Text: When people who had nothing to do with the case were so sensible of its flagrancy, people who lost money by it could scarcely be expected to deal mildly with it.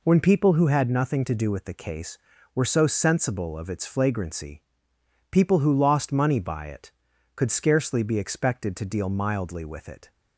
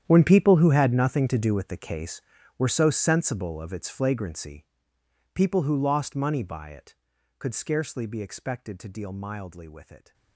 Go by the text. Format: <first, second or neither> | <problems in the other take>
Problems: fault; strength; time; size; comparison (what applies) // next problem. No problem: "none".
first | gets quieter; strong; throughout; 17.5 dB